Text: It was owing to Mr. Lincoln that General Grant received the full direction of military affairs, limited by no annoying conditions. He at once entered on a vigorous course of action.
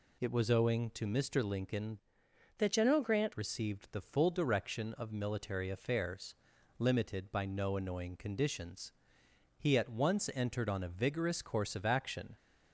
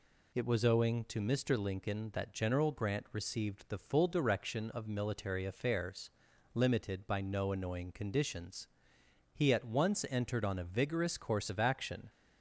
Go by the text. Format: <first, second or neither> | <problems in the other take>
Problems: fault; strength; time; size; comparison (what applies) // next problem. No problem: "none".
second | changes voice from "that" to "Grant"; from 2.5 to 3.3 s; 0.8 s long